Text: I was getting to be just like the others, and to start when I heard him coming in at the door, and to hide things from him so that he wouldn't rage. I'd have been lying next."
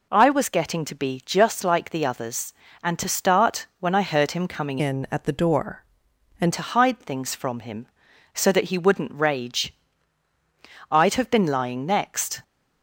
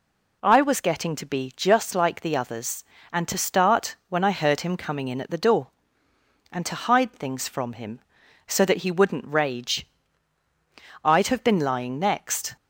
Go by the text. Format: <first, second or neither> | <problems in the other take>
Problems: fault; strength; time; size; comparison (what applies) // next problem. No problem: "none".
second | changes voice from "in" to "and"; from 4.7 to 6.5 s; 1.8 s long